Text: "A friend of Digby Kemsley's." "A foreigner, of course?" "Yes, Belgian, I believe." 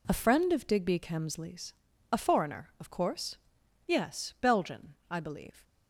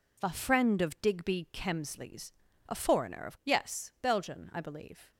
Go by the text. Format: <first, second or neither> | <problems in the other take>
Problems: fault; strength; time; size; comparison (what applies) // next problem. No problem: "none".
first | skips "course"; at 3.4 s